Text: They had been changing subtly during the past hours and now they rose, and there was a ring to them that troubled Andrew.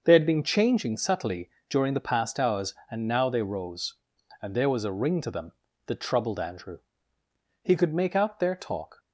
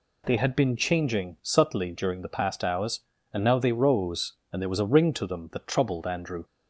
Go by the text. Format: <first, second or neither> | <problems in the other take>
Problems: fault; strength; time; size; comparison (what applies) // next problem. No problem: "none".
second | pauses between "subtly" and "during"; slight; at 1.4 s; 0.20 s long // goes on to say "He could make out their talk"; from 7.6 s on; 1.3 s long